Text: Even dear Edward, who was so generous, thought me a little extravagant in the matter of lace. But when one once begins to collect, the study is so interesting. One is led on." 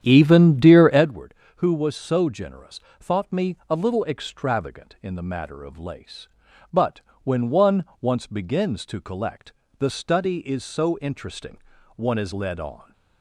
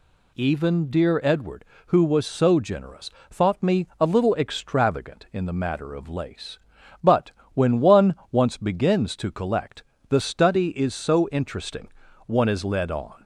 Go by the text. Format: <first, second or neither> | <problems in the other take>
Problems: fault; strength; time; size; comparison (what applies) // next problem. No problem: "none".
second | starts louder than the rest; strong; until 1.1 s; 9.5 dB // pauses between "But" and "when"; slight; at 7.0 s; 0.22 s long; slight in the second // pauses between "one" and "once"; slight; at 7.8 s; 0.16 s long; slight in the second